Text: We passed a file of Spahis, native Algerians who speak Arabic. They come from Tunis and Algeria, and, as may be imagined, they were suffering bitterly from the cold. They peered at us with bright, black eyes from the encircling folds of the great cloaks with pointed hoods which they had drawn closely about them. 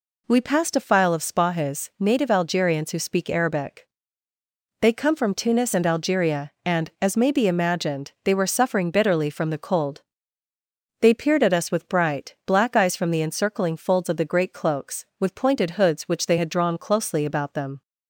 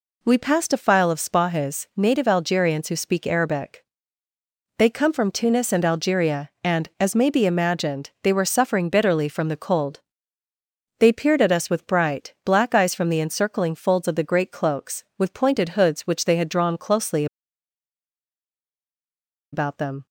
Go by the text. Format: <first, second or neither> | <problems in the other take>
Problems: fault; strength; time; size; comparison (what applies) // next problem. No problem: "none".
first | pauses between "closely" and "about"; strong; at 17.2 s; 2.2 s long